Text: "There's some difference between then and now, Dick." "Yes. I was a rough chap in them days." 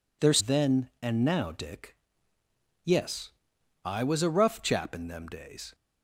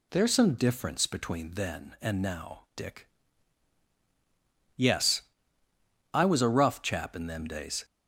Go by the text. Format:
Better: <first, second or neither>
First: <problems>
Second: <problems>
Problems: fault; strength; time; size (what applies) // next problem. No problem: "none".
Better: second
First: skips "some difference between"; at 0.3 s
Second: none